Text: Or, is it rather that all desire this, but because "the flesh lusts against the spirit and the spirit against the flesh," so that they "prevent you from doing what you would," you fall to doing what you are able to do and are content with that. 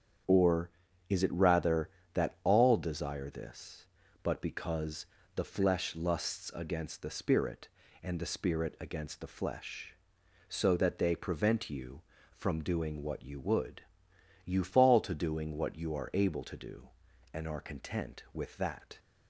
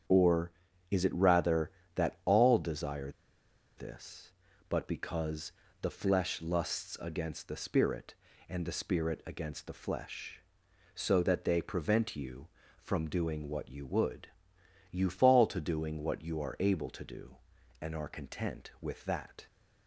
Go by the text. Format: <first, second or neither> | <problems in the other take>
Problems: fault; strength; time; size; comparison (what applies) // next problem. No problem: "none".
first | starts louder than the rest; strong; until 1.4 s; 8 dB; strong in the first // pauses between "desire" and "this"; noticeable; at 3.1 s; 0.66 s long // pauses between "because" and "the"; slight; at 5.5 s; 0.30 s long; slight in the first